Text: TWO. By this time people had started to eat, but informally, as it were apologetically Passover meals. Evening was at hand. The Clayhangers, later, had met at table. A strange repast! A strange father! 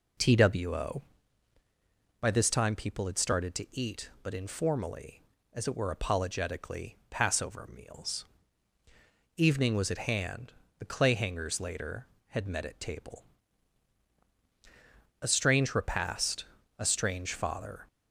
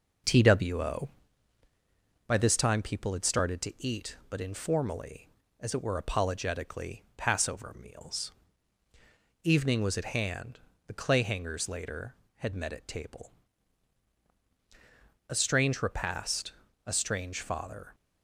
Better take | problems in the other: first | gets quieter; slight; throughout; 2.5 dB

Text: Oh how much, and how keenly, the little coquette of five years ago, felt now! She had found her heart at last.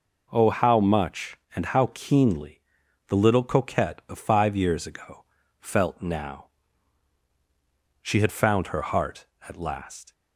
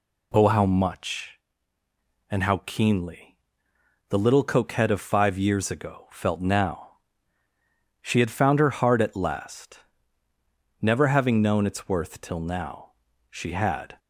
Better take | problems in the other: first | goes on to say "Never having known its worth till now she had"; strong; from 10.8 s on; 3.1 s long

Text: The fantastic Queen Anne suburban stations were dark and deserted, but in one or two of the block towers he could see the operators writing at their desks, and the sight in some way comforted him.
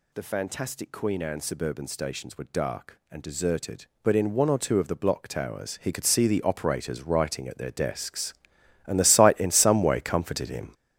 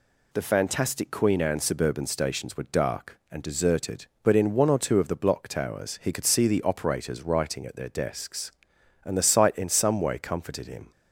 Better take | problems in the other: second | gets louder; strong; throughout; 8.5 dB

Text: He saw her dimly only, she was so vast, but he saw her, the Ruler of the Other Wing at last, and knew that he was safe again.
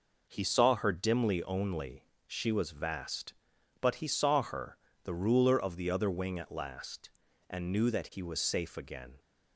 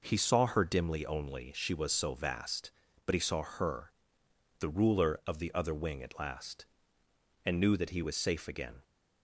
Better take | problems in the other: second | skips "so"; at 2.7 s

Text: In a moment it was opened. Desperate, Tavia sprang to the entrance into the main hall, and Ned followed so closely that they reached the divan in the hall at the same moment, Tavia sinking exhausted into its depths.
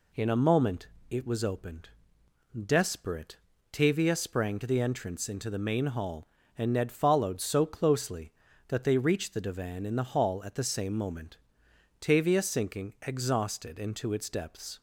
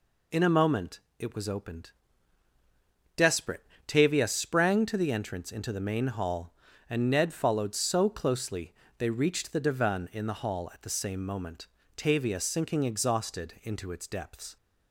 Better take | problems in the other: first | pauses between "moment" and "it"; slight; at 0.9 s; 0.22 s long; slight in the first // skips "that"; at 8.8 s

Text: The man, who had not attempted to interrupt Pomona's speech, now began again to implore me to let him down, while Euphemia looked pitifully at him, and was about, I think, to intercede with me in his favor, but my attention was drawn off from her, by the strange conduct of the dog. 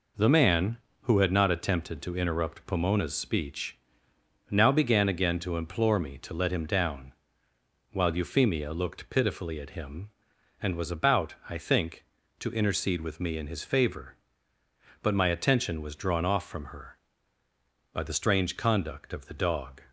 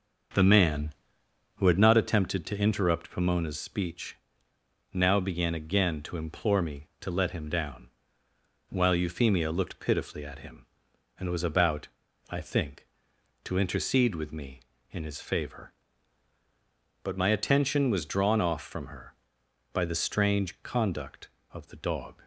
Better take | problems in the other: first | starts louder than the rest; until 1.9 s; 6.5 dB

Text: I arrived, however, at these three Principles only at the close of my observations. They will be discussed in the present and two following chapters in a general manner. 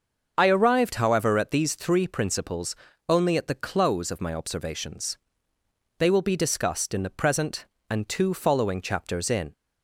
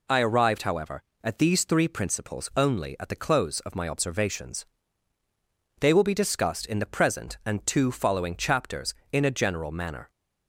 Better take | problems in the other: second | starts louder than the rest; until 1.3 s; 6.5 dB // pauses between "Principles" and "only"; slight; at 2.7 s; 0.34 s long // stops before "a general manner"; at 9.5 s

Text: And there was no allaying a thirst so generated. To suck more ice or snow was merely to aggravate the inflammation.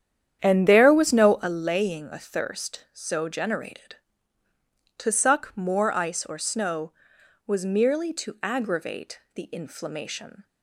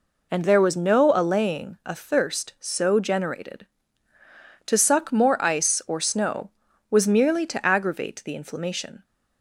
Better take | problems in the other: second | starts louder than the rest; strong; until 1.7 s; 9.5 dB

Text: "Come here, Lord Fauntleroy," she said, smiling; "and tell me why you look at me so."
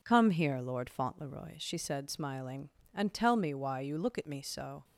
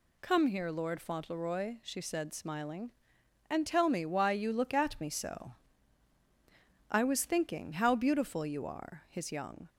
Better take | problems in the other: first | goes on to say "I was thinking how beautiful you are his young"; strong; from 6.9 s on; 2.7 s long

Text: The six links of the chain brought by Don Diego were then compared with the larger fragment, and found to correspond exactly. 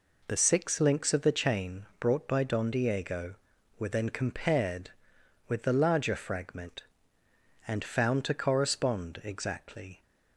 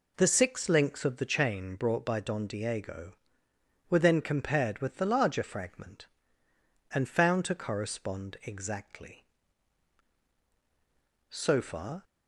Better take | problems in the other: first | goes on to say "So far"; noticeable; from 11.2 s on; 0.74 s long

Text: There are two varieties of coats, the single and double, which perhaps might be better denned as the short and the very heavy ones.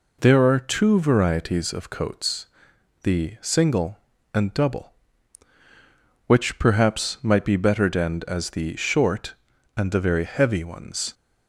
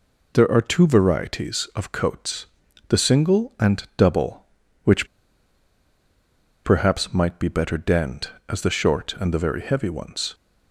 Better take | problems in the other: first | pauses between "which" and "perhaps"; strong; at 5.0 s; 1.6 s long

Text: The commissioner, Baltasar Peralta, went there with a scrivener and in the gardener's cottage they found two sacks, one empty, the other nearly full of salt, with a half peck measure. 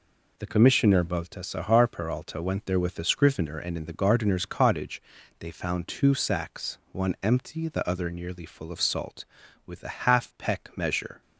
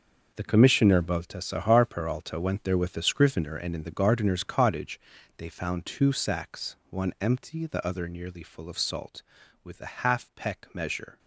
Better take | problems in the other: first | gets quieter; strong; throughout; 12 dB // pauses between "cottage" and "they"; at 4.9 s; 0.38 s long; also in the first

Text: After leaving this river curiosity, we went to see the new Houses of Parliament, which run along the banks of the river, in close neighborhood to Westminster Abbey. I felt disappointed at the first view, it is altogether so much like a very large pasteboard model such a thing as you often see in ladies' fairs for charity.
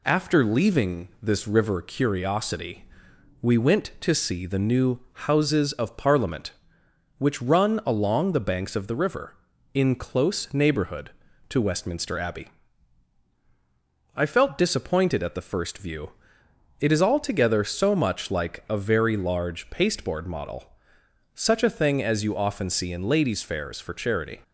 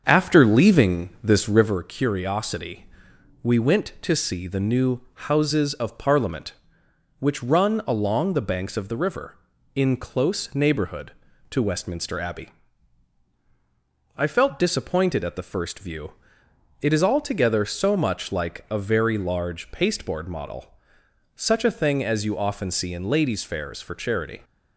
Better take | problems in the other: first | starts louder than the rest; until 1.8 s; 7 dB // pauses between "model" and "such"; noticeable; at 20.7 s; 0.62 s long; noticeable in the first

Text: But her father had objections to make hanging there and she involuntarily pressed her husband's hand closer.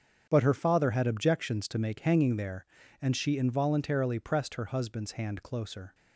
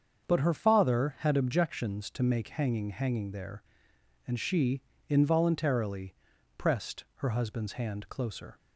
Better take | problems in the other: first | starts louder than the rest; until 1.3 s; 7 dB; strong in the first // says "hanging" twice; at 2.9 s // pauses between "she" and "involuntarily"; slight; at 4.8 s; 0.28 s long // pauses between "involuntarily" and "pressed"; at 6.1 s; 0.42 s long

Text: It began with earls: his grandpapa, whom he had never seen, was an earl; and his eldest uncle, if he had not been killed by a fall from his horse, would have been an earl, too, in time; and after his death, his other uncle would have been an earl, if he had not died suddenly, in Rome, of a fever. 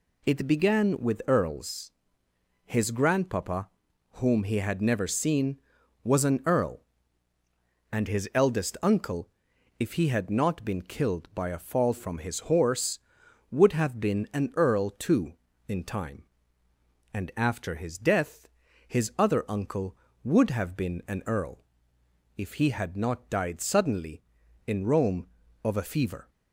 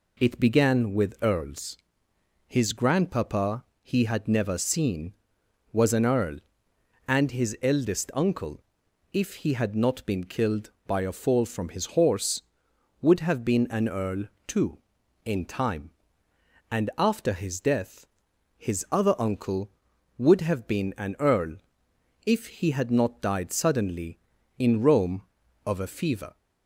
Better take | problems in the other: first | skips "whom"; at 3.7 s

